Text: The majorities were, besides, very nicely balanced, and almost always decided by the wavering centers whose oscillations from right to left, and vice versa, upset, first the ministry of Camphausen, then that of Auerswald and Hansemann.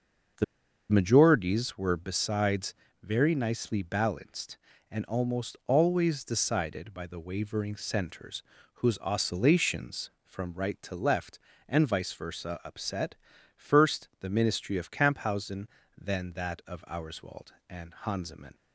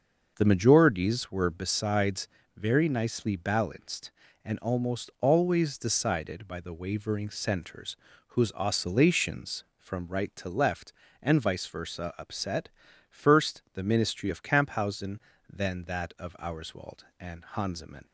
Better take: second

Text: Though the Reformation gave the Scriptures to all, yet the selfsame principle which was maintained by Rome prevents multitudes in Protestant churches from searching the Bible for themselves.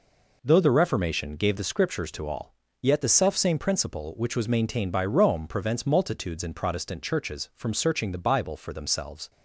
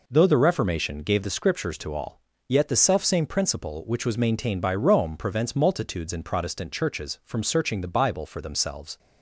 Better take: neither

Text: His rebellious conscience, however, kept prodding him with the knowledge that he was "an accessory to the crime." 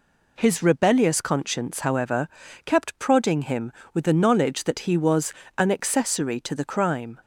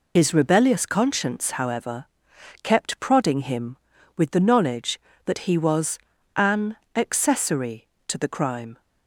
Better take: first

